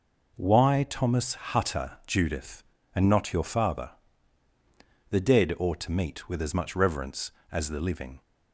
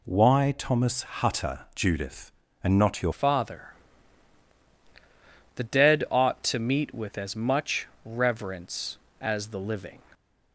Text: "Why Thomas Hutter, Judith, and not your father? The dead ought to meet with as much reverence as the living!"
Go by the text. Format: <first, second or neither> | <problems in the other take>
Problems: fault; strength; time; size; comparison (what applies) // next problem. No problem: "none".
first | changes voice at "father"; from 3.1 s on; 6.9 s long // pauses between "much" and "reverence"; slight; at 7.8 s; 0.18 s long